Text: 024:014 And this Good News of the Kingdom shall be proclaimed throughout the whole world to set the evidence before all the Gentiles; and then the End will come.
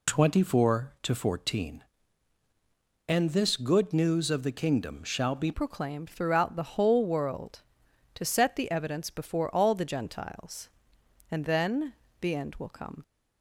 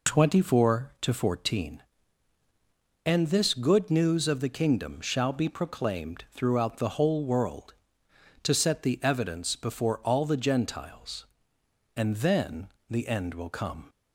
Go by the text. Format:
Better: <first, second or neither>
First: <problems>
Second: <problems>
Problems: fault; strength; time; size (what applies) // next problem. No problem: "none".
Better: second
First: changes voice at "proclaimed"; from 5.5 s on; 7.5 s long // pauses between "then" and "the"; slight; at 11.9 s; 0.28 s long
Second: pauses between "then" and "the"; slight; at 12.6 s; 0.20 s long